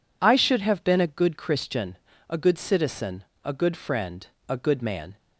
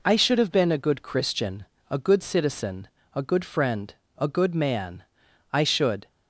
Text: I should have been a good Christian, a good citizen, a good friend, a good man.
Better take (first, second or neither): first